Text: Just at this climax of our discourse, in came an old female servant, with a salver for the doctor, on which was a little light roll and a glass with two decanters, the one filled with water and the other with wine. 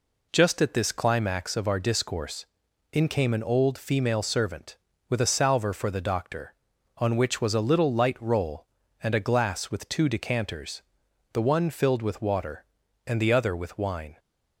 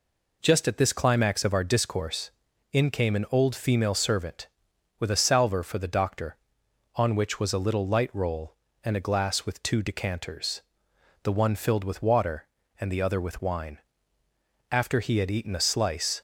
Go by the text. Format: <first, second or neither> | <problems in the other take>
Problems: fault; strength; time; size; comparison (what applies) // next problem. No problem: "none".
first | goes on to say "After he had eaten a slice"; from 14.7 s on; 1.5 s long